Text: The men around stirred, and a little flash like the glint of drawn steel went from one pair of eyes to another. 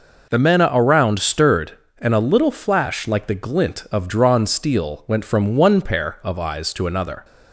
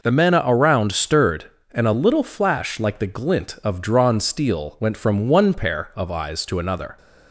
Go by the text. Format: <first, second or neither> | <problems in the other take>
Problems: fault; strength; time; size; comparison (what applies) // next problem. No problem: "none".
neither | none